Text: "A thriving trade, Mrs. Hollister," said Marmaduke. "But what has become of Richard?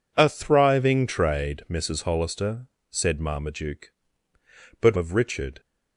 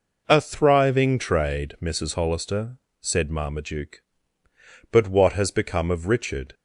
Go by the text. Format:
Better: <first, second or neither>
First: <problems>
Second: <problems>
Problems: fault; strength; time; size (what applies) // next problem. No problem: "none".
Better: second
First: skips "what has become"; at 4.9 s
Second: none